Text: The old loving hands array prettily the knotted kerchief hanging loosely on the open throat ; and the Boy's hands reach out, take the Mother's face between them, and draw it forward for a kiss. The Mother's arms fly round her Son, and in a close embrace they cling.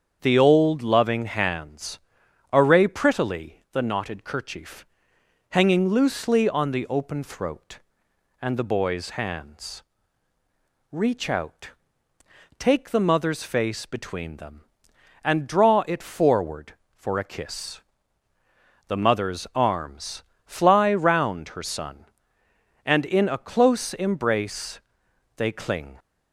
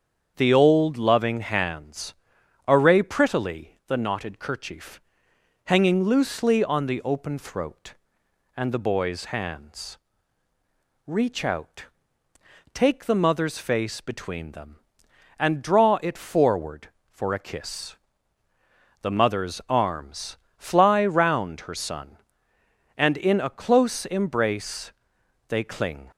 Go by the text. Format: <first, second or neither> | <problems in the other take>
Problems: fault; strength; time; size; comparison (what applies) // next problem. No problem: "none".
neither | starts louder than the rest; strong; the same in both // pauses between "hands" and "array"; noticeable; the same in both // pauses between "kerchief" and "hanging"; noticeable; the same in both // pauses between "hands" and "reach"; the same in both // pauses between "arms" and "fly"; slight; the same in both // pauses between "embrace" and "they"; noticeable; the same in both